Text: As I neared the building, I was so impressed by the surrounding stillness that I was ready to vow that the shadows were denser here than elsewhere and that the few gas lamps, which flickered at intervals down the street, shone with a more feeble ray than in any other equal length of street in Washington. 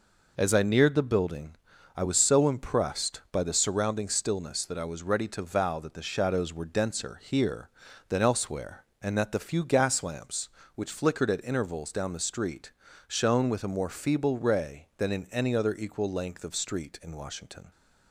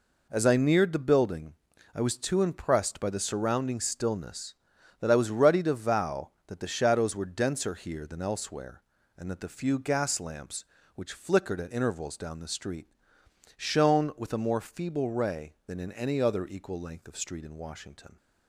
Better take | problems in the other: first | says "too" for "so"; at 2.1 s

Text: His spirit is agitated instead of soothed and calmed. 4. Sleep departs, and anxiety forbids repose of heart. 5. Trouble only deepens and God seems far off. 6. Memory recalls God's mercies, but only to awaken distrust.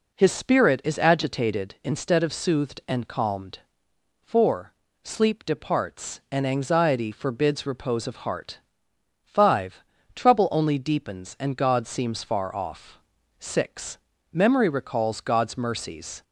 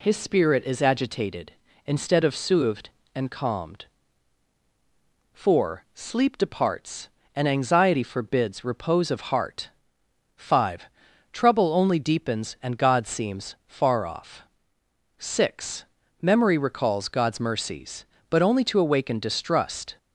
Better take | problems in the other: second | stops before "but only to awaken distrust"; at 16.2 s

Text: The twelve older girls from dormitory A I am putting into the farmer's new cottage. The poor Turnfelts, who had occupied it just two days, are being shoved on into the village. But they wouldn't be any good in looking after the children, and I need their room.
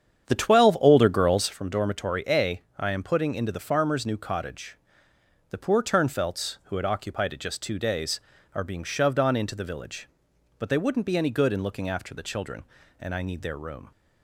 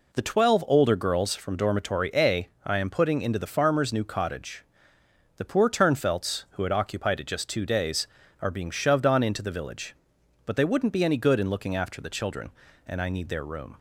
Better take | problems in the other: second | starts louder than the rest; strong; until 1.6 s; 8.5 dB // pauses between "A" and "I"; slight; at 2.6 s; 0.16 s long; slight in the second

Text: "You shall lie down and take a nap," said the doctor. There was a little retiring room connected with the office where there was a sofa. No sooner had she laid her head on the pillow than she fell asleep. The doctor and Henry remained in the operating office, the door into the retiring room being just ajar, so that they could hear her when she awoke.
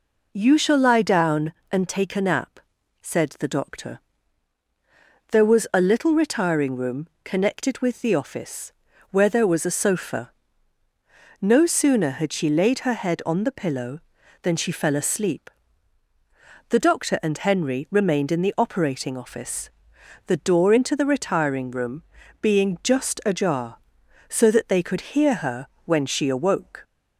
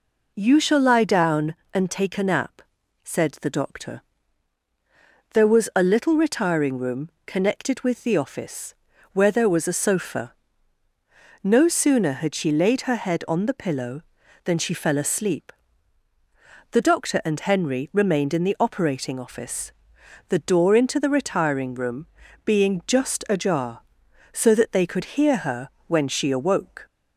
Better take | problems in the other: neither | pauses between "room" and "connected"; slight; the same in both // pauses between "office" and "where"; the same in both // pauses between "room" and "being"; the same in both // pauses between "her" and "when"; slight; the same in both

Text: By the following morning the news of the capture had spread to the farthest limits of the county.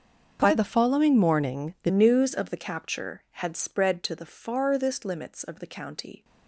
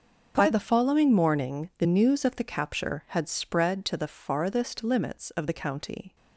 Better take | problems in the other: second | starts louder than the rest; until 1.4 s; 7 dB; also in the second // changes voice at "news"; from 1.9 s on; 4.3 s long

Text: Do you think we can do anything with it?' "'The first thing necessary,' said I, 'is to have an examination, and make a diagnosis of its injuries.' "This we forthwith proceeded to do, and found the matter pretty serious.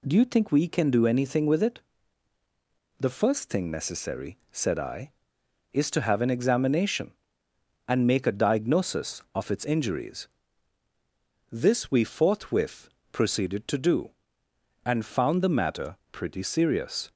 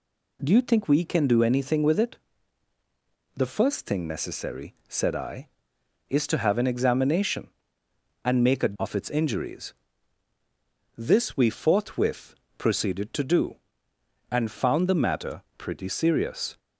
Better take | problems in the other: first | skips "diagnosis"; at 8.7 s // pauses between "forthwith" and "proceeded"; slight; at 12.3 s; 0.24 s long; slight in the first // pauses between "matter" and "pretty"; slight; at 15.4 s; 0.16 s long; slight in the first

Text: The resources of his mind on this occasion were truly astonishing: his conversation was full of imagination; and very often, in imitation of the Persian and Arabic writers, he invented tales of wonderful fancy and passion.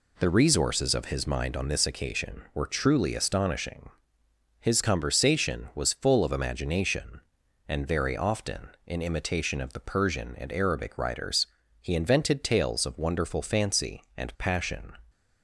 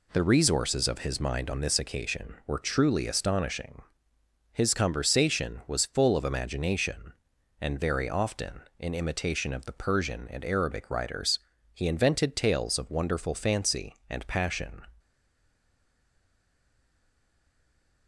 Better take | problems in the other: first | stays silent after the last word; strong; from 14.9 s on; 3.1 s long

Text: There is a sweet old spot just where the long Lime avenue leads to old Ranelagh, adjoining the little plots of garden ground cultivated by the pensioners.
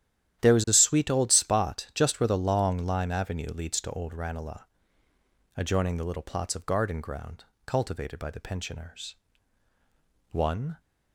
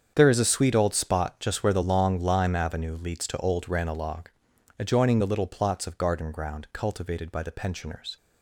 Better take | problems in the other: second | starts louder than the rest; strong; until 1.4 s; 11.5 dB; strong in the second // pauses between "ground" and "cultivated"; slight; at 7.4 s; 0.22 s long // goes on to say "One"; slight; from 10.3 s on; 0.48 s long

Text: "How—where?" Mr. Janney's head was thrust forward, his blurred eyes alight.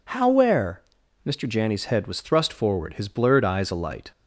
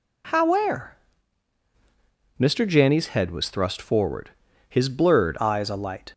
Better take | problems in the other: first | changes voice at "eyes"; from 5.4 s on; 0.7 s long

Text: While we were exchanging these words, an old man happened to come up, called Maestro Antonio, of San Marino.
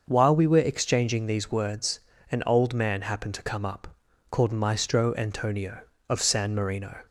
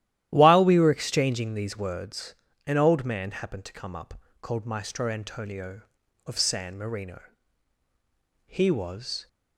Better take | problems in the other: first | starts louder than the rest; strong; until 1.3 s; 12.5 dB; noticeable in the first // goes on to say "He was"; noticeable; from 8.4 s on; 0.80 s long

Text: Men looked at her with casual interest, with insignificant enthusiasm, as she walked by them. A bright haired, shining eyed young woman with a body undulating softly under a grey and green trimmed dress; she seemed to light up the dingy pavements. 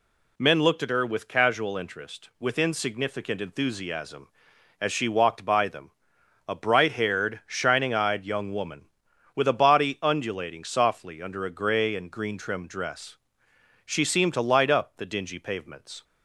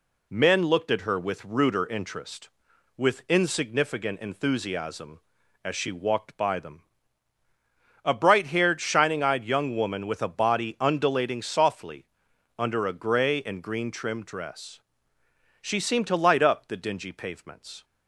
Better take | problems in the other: first | says "ruder" for "casual"; at 1.4 s // pauses between "softly" and "under"; noticeable; at 12.0 s; 0.52 s long

